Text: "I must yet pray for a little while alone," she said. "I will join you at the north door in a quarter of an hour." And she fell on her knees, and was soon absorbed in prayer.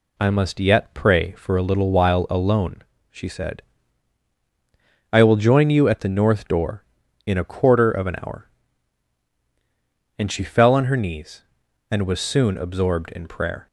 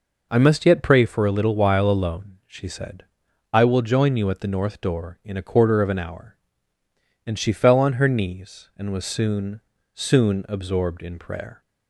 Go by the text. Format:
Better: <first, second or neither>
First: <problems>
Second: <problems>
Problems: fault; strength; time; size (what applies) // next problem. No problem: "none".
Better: first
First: none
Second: says "soon" twice; at 9.9 s